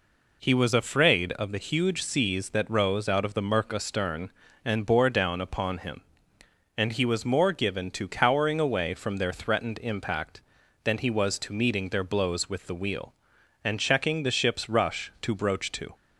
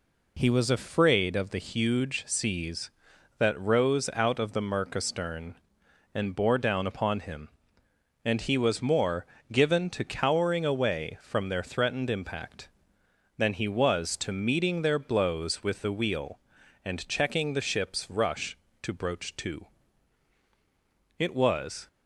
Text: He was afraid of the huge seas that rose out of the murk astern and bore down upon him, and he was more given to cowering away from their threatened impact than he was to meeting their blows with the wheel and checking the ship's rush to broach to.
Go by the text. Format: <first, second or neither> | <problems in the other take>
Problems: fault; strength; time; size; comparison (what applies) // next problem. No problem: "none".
first | pauses between "more" and "given"; slight; at 9.2 s; 0.26 s long // goes on to say "It was"; noticeable; from 21.1 s on; 0.70 s long